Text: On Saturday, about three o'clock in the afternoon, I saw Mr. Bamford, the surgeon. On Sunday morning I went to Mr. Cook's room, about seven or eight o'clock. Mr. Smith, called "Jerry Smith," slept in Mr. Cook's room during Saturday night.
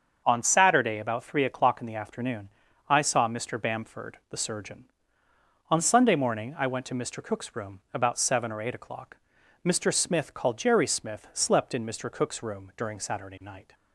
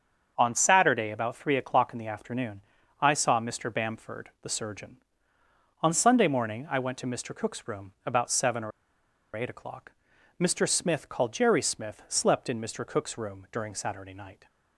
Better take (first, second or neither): first